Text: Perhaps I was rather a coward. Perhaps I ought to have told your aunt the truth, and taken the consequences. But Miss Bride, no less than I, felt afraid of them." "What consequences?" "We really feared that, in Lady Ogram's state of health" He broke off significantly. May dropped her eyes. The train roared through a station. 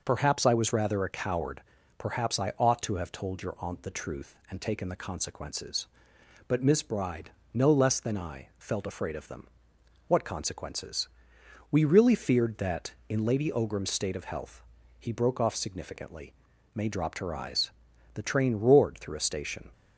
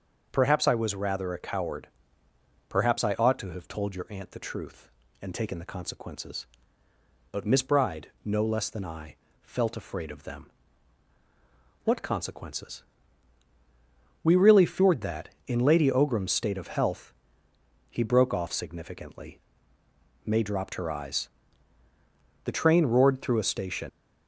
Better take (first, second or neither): first